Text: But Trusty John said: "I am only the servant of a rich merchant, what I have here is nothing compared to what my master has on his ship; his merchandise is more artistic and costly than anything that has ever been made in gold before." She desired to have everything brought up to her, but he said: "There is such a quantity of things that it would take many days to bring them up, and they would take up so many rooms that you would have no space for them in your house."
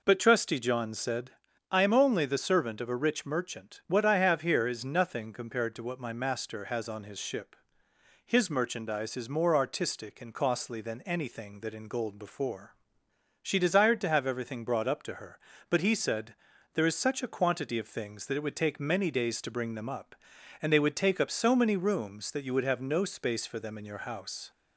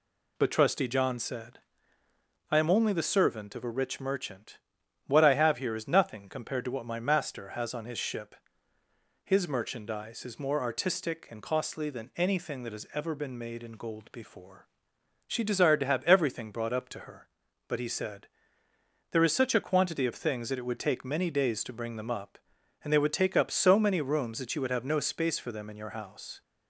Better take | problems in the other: second | skips "has ever been made"; at 11.7 s

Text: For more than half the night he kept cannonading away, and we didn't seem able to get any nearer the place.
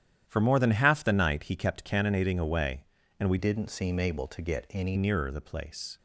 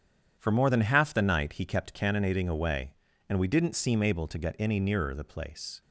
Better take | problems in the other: second | starts louder than the rest; strong; until 1.2 s; 10.5 dB; strong in the second // changes voice from "didn't" to "any"; from 3.3 to 4.9 s; 1.6 s long

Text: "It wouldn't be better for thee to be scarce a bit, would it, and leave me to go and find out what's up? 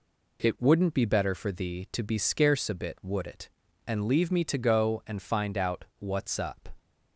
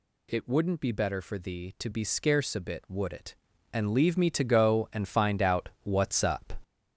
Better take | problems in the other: first | gets louder; noticeable; throughout; 6 dB

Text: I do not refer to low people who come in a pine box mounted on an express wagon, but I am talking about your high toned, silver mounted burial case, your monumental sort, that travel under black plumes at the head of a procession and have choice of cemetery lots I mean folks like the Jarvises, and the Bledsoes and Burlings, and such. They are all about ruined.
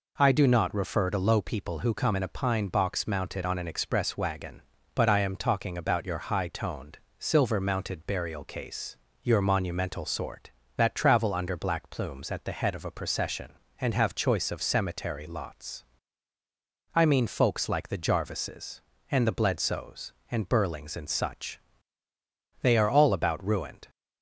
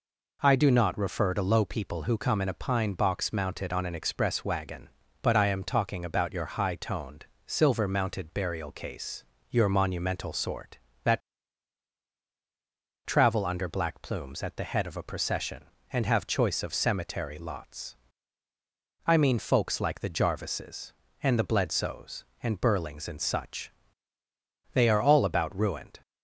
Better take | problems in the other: first | pauses between "that" and "travel"; strong; at 11.2 s; 1.8 s long // pauses between "lots" and "I"; at 17.9 s; 1.1 s long; also in the first

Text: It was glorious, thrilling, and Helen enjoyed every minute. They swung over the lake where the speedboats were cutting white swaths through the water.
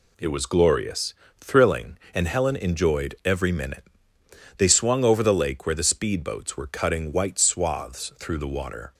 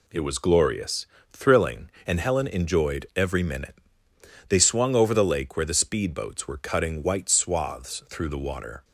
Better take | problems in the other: neither | none

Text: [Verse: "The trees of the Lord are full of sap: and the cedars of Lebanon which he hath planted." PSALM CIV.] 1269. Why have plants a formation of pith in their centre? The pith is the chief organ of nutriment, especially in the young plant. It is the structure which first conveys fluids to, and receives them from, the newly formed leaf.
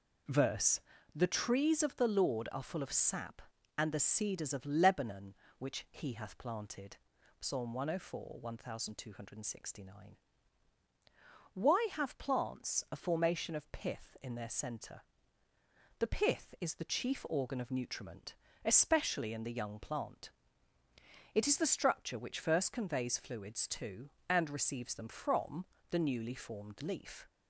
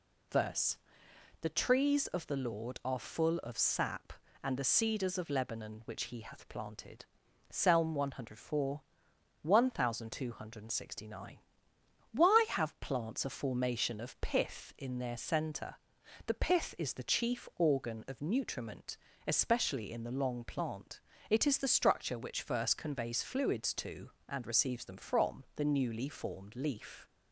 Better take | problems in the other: first | says "long" for "young"; at 20.1 s

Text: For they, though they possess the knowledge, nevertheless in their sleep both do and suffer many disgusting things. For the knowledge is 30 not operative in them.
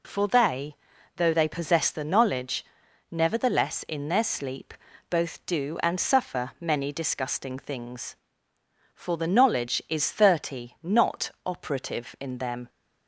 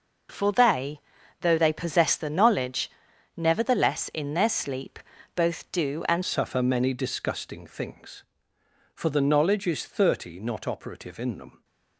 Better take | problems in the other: first | pauses between "sleep" and "both"; slight; at 5.0 s; 0.34 s long; slight in the first // changes voice at "suffer"; from 6.2 s on; 5.4 s long

